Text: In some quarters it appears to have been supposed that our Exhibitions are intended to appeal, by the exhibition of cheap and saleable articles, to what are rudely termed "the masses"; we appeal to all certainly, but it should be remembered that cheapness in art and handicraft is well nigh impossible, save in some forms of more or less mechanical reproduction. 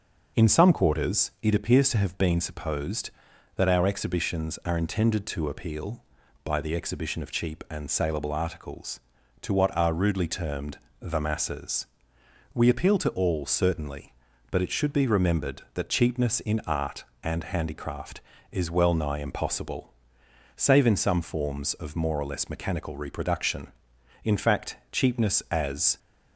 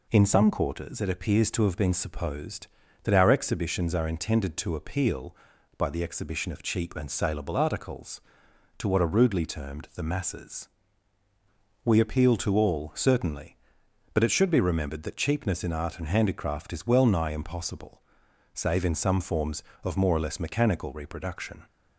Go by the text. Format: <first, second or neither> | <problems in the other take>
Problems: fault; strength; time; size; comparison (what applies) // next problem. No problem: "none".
second | pauses between "termed" and "the"; slight; at 10.7 s; 0.20 s long // goes on to say "In fact cheapness as"; strong; from 24.2 s on; 1.7 s long